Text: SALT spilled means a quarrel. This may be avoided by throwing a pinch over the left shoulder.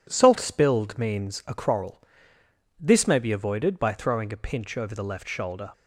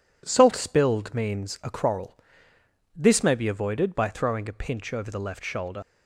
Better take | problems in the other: first | leaves "shoulder" unfinished; at 5.8 s; 55 ms

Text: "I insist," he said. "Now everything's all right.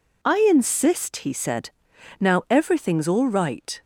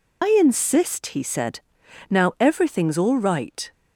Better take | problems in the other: first | loses the start of "I"; at 0.2 s; 80 ms

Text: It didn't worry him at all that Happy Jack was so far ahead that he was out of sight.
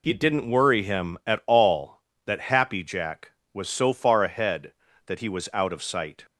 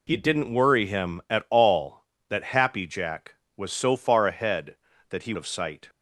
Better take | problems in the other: first | skips "was out"; at 5.3 s

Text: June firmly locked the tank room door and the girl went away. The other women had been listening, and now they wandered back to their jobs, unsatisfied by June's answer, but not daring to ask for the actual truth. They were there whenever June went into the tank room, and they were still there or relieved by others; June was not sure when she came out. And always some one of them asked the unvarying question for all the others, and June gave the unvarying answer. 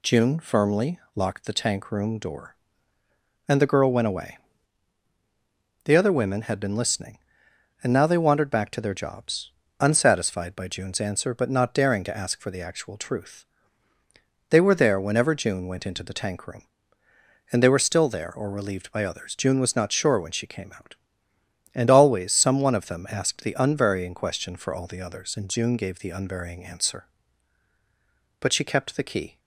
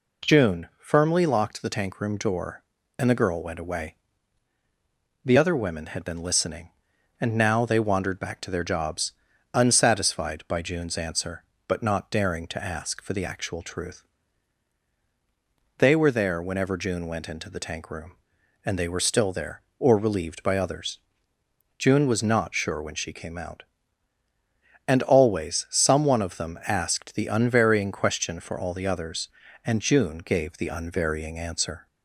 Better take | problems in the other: second | pauses between "firmly" and "locked"; slight; at 0.9 s; 0.16 s long // goes on to say "But she kept the key"; noticeable; from 28.4 s on; 0.98 s long

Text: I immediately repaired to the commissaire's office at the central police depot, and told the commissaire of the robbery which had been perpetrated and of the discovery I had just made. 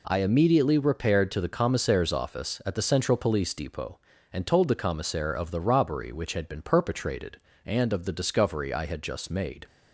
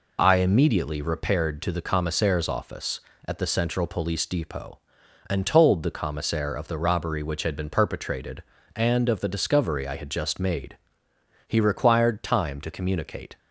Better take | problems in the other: first | goes on to say "He required time to communicate"; strong; from 11.4 s on; 1.9 s long

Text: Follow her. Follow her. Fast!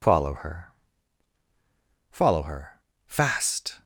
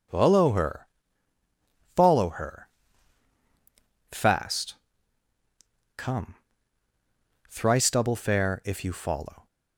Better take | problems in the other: first | goes on to say "Come Thrice double fare if you follow"; strong; from 5.9 s on; 3.5 s long

